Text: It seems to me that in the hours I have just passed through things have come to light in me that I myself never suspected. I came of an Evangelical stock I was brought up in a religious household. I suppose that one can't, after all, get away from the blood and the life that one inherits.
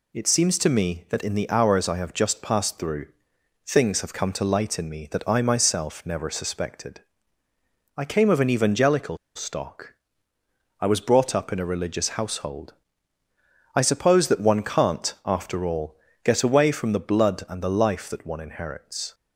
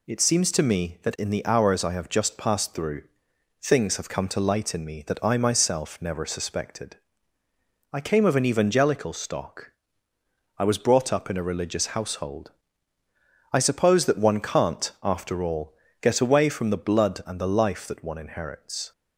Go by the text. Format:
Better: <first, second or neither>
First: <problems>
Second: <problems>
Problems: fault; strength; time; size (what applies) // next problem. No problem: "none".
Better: second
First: pauses between "through" and "things"; noticeable; at 3.0 s; 0.58 s long // pauses between "Evangelical" and "stock"; slight; at 9.1 s; 0.18 s long // pauses between "stock" and "I"; noticeable; at 9.9 s; 0.86 s long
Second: pauses between "through" and "things"; noticeable; at 3.0 s; 0.58 s long // pauses between "stock" and "I"; noticeable; at 9.7 s; 0.86 s long